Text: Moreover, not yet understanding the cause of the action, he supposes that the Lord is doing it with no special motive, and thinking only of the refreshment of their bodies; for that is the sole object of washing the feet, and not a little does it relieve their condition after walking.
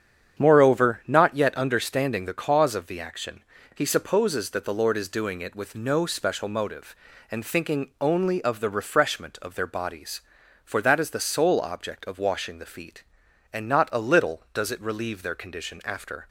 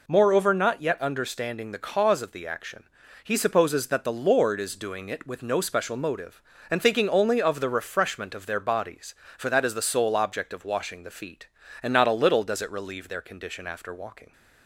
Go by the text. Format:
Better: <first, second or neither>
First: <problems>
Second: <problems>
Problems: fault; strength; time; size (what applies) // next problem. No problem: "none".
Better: second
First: starts louder than the rest; strong; until 1.4 s; 8 dB // stops before "walking"; at 16.2 s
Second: none